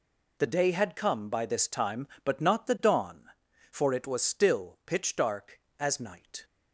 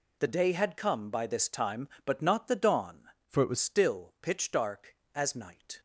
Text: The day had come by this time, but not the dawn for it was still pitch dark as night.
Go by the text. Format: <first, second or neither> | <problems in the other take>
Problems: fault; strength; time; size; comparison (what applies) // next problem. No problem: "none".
first | changes voice from "for" to "was"; from 3.2 to 3.5 s; 0.3 s long